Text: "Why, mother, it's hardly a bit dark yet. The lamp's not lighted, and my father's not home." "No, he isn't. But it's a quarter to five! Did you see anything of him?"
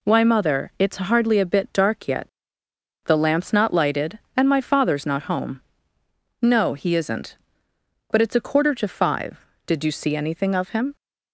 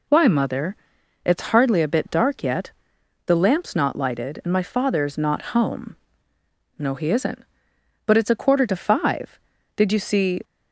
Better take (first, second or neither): first